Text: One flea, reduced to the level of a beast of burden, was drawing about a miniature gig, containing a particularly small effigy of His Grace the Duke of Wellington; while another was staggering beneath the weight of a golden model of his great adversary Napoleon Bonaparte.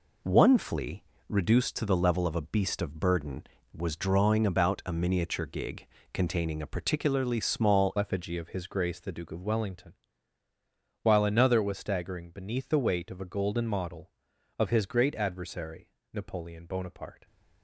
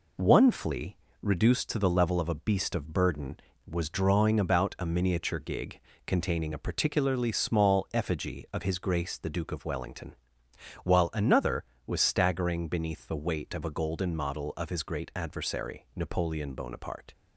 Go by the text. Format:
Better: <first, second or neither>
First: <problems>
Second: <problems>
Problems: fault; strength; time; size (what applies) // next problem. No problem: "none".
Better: second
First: changes voice at "effigy"; from 7.9 s on; 9.3 s long // pauses between "adversary" and "Napoleon"; slight; at 15.8 s; 0.24 s long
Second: none